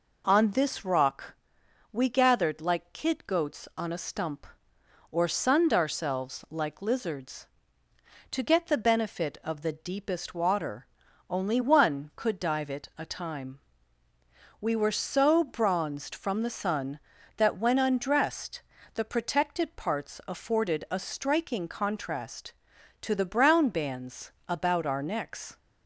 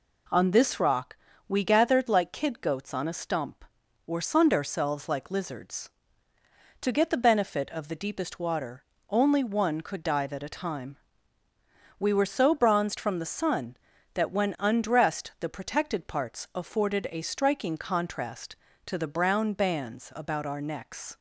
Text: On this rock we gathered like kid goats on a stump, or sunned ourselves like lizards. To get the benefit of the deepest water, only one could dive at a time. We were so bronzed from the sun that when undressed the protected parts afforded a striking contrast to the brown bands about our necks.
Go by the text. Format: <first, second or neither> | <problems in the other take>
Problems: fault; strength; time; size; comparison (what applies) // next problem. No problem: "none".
second | pauses between "rock" and "we"; noticeable; at 1.3 s; 0.56 s long; slight in the second // says "it" for "at"; at 12.6 s // pauses between "undressed" and "the"; slight; at 18.6 s; 0.32 s long // pauses between "bands" and "about"; slight; at 24.3 s; 0.16 s long